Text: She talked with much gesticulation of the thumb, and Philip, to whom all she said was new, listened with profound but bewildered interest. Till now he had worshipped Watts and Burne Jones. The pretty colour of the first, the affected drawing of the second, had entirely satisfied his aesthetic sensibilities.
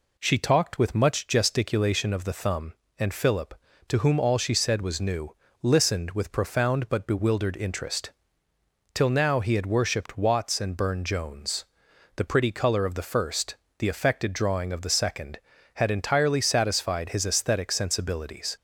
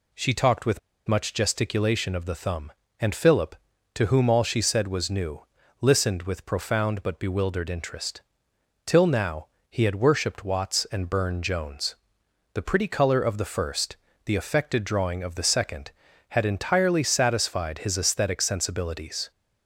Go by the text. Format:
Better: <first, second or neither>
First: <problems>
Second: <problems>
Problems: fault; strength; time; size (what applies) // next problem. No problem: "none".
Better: first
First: none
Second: pauses between "with" and "much"; slight; at 0.7 s; 0.29 s long // pauses between "now" and "he"; slight; at 9.4 s; 0.22 s long